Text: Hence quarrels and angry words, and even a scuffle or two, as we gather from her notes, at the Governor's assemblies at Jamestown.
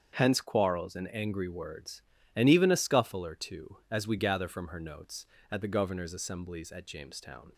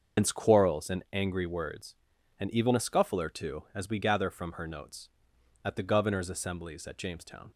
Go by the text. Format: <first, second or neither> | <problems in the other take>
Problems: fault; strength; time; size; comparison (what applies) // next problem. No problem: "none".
first | loses the start of "Hence"; at 0.1 s; 105 ms // starts louder than the rest; until 1.2 s; 6.5 dB; strong in the first